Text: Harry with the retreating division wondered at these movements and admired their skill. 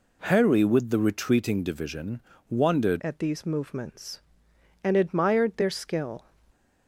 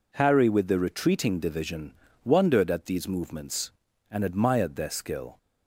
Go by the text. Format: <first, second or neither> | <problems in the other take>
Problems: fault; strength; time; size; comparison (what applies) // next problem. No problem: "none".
second | pauses between "division" and "wondered"; slight; at 2.2 s; 0.30 s long; slight in the second // changes voice at "at"; from 3.0 s on; 3.2 s long